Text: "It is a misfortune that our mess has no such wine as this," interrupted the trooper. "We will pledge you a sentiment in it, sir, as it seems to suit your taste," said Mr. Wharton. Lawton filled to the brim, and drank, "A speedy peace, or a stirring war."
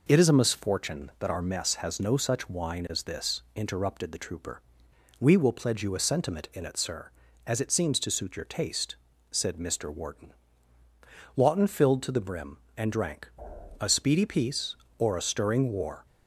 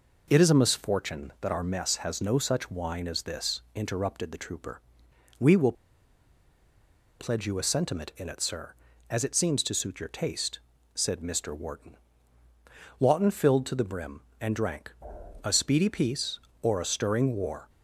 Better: first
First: none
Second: pauses between "will" and "pledge"; strong; at 5.7 s; 1.4 s long

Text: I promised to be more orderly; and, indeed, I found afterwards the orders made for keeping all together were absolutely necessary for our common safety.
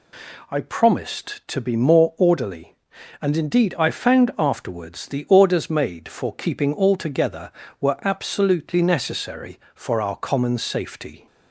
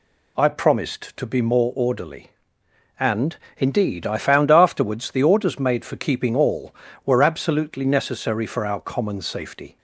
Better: first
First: none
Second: skips "together"; at 6.9 s

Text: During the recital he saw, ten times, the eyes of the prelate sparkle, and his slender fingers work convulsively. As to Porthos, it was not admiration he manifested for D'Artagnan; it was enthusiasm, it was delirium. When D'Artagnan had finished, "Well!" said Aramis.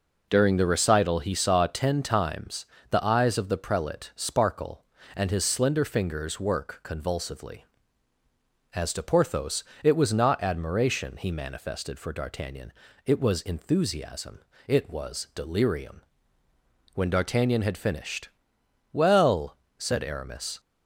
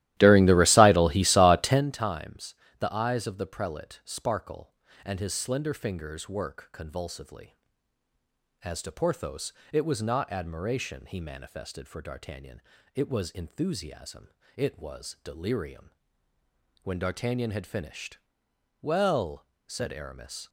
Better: first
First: none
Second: starts louder than the rest; strong; until 1.9 s; 15.5 dB

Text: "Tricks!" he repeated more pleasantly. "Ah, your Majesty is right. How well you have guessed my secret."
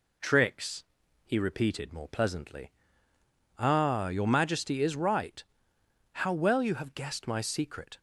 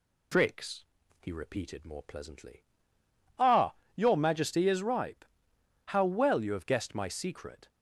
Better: first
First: none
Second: says "ripe" for "right"; at 4.8 s

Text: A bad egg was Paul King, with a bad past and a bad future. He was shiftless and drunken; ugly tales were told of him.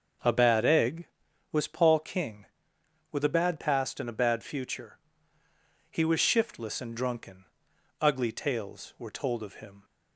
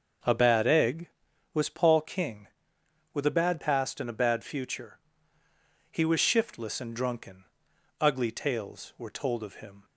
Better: neither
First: starts louder than the rest; until 1.6 s; 6.5 dB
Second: starts louder than the rest; until 1.6 s; 6.5 dB

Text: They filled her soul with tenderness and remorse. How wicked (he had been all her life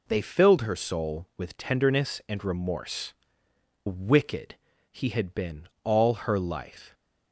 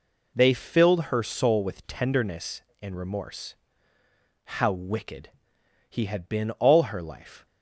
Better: second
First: skips "How"; at 3.4 s // pauses between "been" and "all"; slight; at 5.6 s; 0.16 s long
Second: none

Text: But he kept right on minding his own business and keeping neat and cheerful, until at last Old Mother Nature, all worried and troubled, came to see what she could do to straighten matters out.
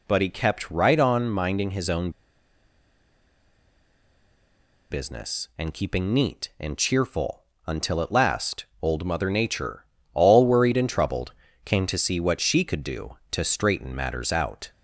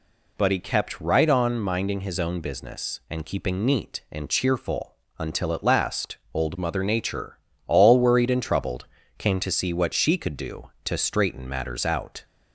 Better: second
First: pauses between "own" and "business"; strong; at 2.0 s; 2.8 s long // pauses between "last" and "Old"; slight; at 8.6 s; 0.16 s long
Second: pauses between "last" and "Old"; slight; at 6.1 s; 0.16 s long

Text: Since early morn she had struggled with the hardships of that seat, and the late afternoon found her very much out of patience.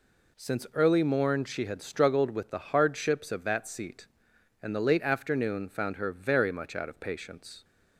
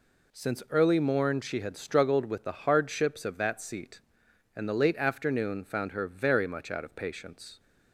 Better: neither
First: none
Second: none

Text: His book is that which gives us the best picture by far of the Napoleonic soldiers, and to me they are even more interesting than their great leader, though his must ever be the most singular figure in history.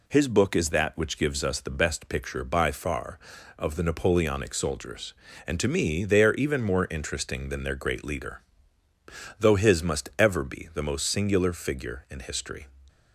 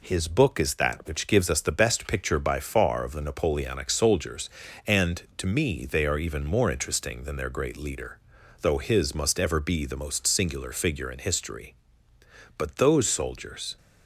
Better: first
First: none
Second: goes on to say "But those soldiers"; noticeable; from 12.5 s on; 1.2 s long

